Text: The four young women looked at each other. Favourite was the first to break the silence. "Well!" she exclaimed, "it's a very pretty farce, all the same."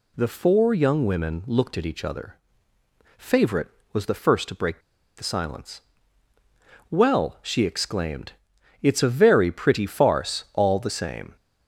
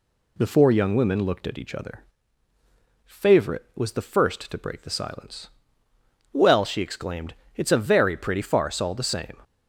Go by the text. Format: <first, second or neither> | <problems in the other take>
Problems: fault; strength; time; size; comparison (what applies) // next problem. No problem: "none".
second | pauses between "break" and "the"; at 4.7 s; 0.37 s long